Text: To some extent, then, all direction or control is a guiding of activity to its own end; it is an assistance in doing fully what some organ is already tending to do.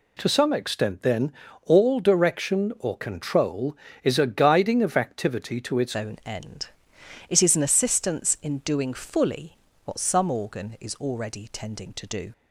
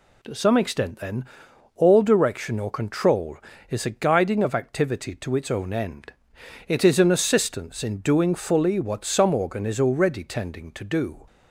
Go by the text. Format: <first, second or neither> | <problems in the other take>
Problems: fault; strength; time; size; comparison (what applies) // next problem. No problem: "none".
second | changes voice at "own"; from 5.9 s on; 6.4 s long // pauses between "fully" and "what"; slight; at 9.5 s; 0.32 s long